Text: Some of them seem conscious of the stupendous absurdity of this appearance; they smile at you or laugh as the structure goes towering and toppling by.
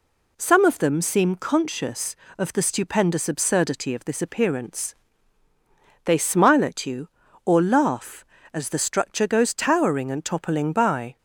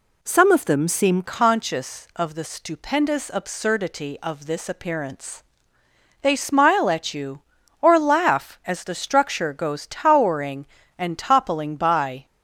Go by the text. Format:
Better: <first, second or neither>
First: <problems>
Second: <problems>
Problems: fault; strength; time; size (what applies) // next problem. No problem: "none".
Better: first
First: none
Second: changes voice at "conscious"; from 1.2 s on; 11.0 s long